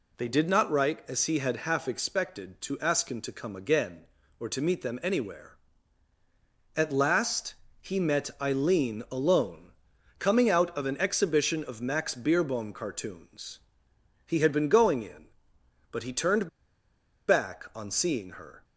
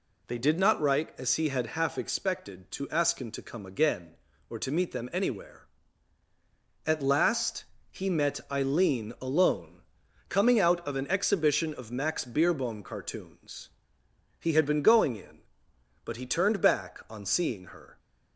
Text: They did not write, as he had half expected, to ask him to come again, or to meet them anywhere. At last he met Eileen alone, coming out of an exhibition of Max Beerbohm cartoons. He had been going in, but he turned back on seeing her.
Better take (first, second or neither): second